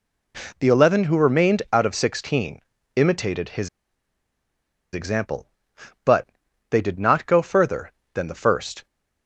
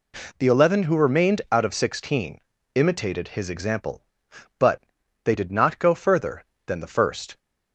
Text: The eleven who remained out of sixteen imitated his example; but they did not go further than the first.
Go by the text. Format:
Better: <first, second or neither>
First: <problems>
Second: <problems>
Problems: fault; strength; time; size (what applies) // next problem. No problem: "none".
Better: second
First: pauses between "sixteen" and "imitated"; slight; at 2.5 s; 0.34 s long // pauses between "his" and "example"; strong; at 3.6 s; 1.2 s long // pauses between "but" and "they"; at 6.2 s; 0.44 s long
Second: pauses between "sixteen" and "imitated"; slight; at 2.3 s; 0.34 s long // pauses between "but" and "they"; at 4.7 s; 0.44 s long